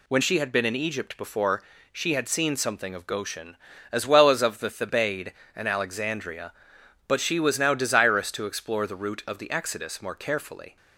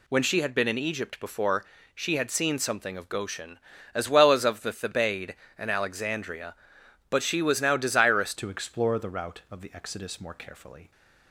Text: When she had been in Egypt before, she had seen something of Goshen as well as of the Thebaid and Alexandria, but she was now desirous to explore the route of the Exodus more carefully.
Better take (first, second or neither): first